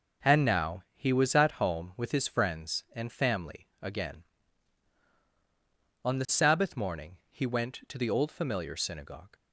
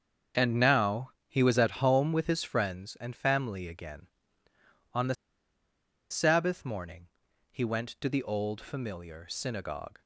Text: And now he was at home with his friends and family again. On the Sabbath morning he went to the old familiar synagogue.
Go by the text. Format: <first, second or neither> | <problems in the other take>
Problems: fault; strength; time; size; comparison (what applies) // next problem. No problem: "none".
first | starts louder than the rest; until 1.5 s; 7 dB // pauses between "the" and "Sabbath"; noticeable; at 5.1 s; 0.96 s long // pauses between "morning" and "he"; at 7.0 s; 0.42 s long